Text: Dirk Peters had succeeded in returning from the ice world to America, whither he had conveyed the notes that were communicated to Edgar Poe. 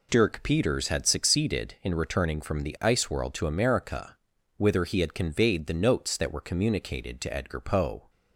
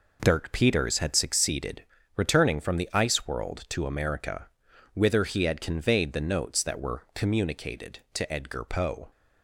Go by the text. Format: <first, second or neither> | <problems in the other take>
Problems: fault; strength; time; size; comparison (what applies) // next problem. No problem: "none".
first | skips "in"; at 1.9 s